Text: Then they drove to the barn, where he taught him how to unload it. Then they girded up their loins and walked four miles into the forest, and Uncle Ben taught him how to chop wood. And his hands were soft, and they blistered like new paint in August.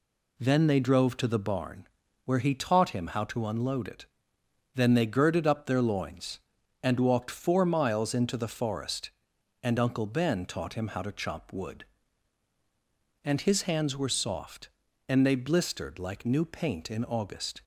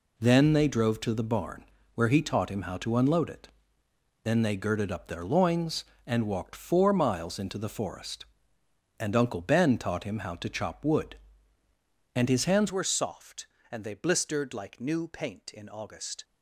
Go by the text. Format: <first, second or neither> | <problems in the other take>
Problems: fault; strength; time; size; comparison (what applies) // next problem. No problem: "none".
first | changes voice at "were"; from 12.7 s on; 3.5 s long